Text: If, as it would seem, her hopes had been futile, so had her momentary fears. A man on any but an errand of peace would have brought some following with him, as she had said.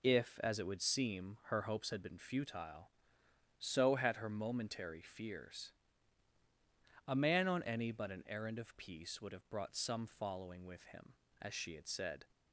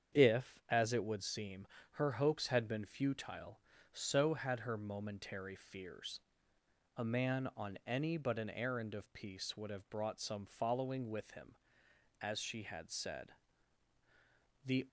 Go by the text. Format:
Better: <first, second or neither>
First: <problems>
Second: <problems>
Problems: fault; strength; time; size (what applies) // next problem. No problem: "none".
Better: first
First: none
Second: starts louder than the rest; strong; until 1.2 s; 8 dB // goes on to say "The"; slight; from 14.6 s on; 0.24 s long